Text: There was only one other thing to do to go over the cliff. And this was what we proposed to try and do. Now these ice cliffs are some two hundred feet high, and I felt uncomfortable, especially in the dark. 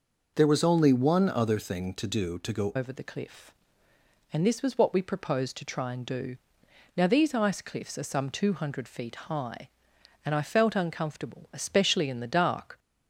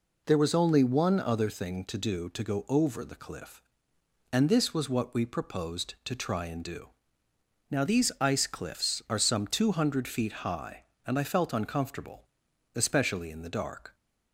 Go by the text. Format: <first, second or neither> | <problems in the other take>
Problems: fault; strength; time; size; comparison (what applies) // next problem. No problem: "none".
second | changes voice at "over"; from 2.7 s on; 10.0 s long